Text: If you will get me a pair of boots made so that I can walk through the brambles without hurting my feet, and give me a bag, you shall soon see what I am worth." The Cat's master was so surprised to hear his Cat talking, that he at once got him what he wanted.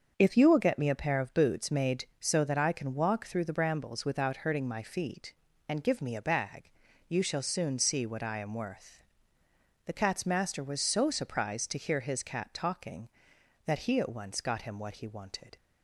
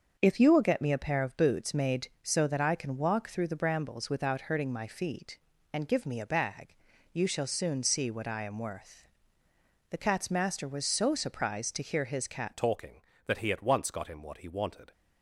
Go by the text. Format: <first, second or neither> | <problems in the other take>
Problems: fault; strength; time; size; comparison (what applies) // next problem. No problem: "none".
first | starts louder than the rest; until 1.1 s; 6.5 dB; also in the first // changes voice at "talking"; from 12.5 s on; 2.4 s long